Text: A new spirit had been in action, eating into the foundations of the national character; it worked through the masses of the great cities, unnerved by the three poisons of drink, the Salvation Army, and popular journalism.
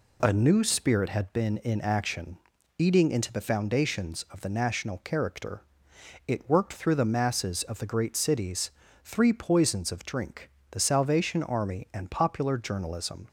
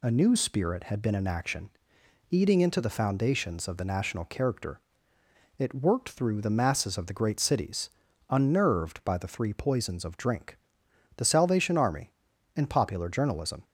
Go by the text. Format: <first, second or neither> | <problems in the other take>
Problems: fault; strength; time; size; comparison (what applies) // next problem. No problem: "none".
second | skips "unnerved by the"; at 8.8 s